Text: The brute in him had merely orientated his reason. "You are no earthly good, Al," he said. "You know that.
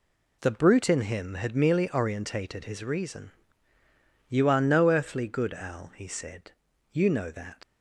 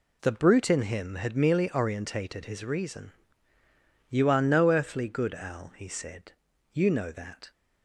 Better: second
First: leaves "that" unfinished; at 7.6 s; 75 ms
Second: none

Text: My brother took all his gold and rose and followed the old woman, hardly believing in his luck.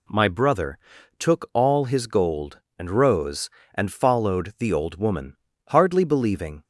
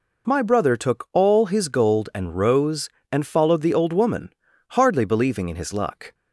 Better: second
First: pauses between "brother" and "took"; at 0.7 s; 0.42 s long // stops before "in his luck"; at 6.6 s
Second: none

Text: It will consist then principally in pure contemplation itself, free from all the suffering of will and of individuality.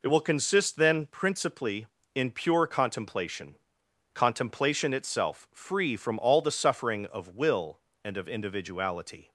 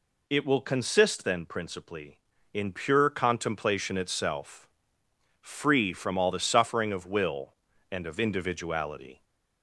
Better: second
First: says "contemplation" twice; at 4.1 s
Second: none

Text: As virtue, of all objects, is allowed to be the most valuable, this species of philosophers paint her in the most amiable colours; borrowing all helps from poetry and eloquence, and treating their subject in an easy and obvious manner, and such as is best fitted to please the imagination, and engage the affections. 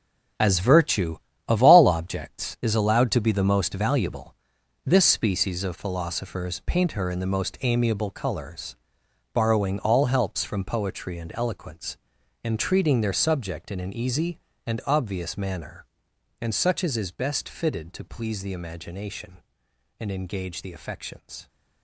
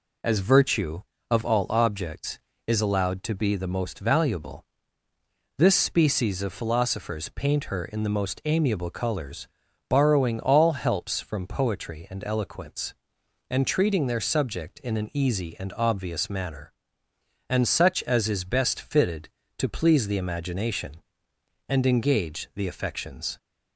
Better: second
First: gets quieter; strong; throughout; 10.5 dB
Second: none

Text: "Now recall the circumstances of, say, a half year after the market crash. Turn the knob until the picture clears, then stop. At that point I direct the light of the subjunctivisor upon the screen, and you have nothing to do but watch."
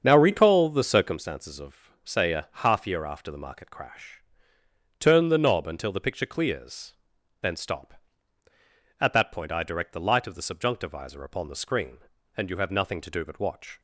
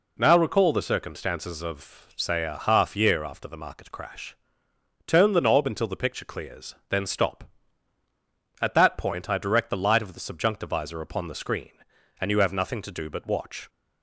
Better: second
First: starts louder than the rest; strong; until 1.2 s; 7 dB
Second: none

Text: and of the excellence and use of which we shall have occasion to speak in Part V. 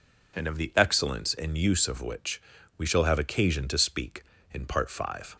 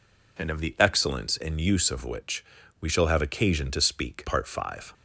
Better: first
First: pauses between "which" and "we"; slight; at 2.4 s; 0.36 s long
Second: pauses between "which" and "we"; slight; at 2.4 s; 0.36 s long // skips "in"; at 4.2 s

